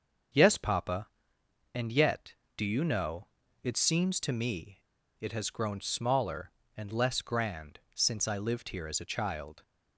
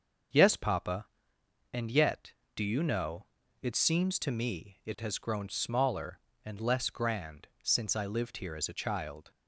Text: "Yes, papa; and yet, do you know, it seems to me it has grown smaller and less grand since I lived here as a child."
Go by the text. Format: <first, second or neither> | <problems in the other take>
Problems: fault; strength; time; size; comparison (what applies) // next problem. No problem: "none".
second | starts louder than the rest; until 2.0 s; 6.5 dB; also in the second // pauses between "me" and "it"; at 4.7 s; 0.40 s long // pauses between "grand" and "since"; slight; at 7.7 s; 0.16 s long; slight in the second